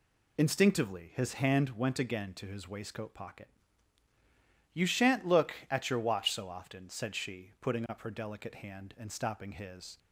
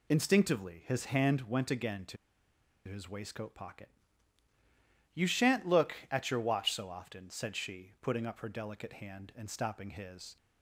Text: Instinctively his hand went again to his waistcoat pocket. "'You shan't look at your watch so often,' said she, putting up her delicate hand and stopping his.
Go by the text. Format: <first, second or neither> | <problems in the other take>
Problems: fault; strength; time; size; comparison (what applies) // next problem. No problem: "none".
first | pauses between "to" and "his"; noticeable; at 2.1 s; 0.69 s long